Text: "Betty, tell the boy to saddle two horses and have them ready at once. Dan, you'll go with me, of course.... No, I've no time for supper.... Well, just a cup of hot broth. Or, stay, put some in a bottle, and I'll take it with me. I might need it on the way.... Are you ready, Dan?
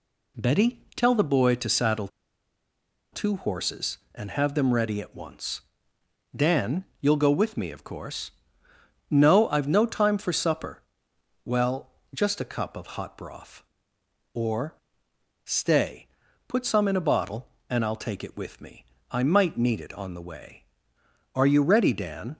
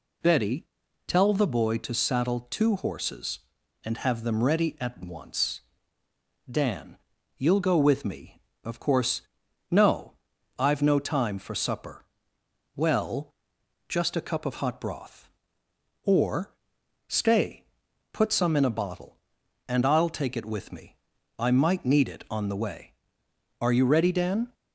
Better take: second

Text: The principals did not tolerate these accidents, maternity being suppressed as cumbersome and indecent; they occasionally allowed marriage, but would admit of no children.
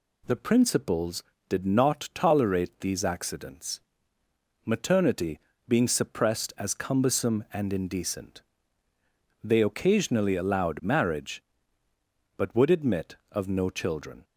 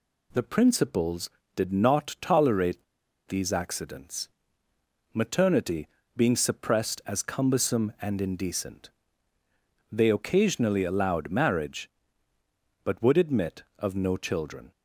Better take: first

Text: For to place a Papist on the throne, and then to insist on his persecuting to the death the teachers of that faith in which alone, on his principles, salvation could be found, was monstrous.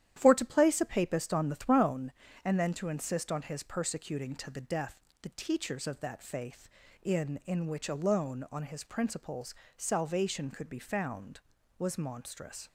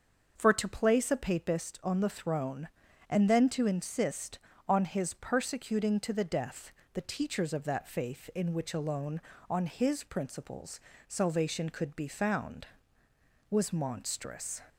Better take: second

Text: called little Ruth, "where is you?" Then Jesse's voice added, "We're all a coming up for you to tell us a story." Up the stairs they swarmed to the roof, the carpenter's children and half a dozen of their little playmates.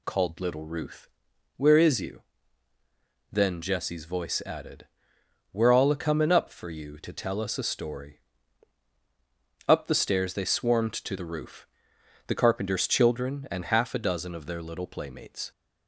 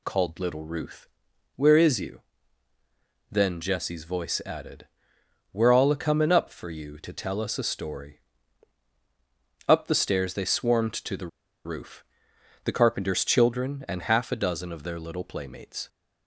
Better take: first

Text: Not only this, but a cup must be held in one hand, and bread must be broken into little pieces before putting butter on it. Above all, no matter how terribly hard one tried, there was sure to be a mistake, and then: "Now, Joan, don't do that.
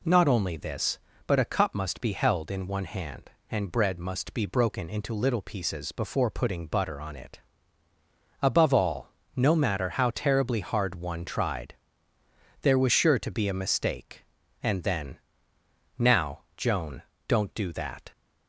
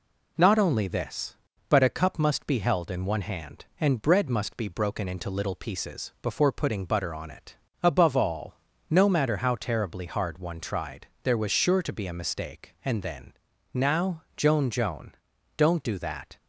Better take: first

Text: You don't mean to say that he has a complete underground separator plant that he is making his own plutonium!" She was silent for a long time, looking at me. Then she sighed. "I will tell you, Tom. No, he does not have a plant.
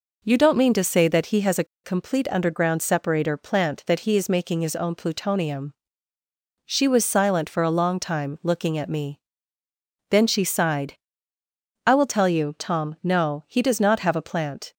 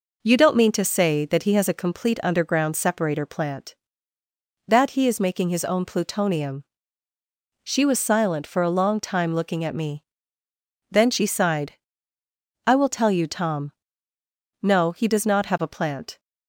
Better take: second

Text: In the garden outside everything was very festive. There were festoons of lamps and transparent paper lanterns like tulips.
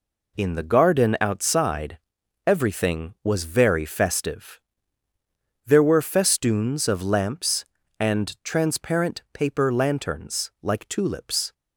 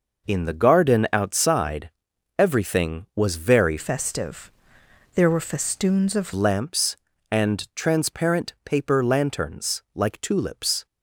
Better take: first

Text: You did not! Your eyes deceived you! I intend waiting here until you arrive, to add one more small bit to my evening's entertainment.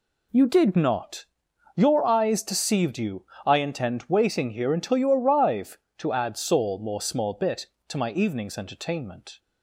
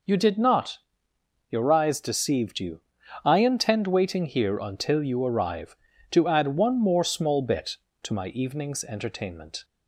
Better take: second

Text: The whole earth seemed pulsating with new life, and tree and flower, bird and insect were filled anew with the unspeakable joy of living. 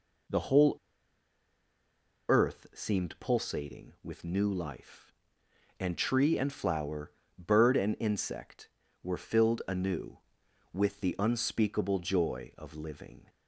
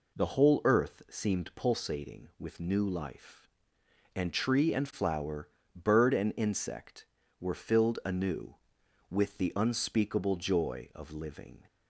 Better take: second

